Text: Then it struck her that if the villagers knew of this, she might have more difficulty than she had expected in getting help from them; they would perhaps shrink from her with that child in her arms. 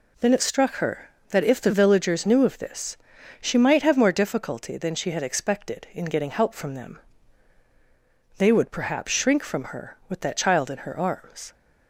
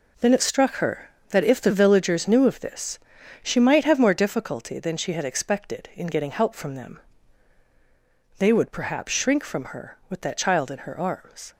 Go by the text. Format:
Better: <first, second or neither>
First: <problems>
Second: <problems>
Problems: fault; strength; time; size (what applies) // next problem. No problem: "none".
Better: first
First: none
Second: gets quieter; strong; throughout; 9.5 dB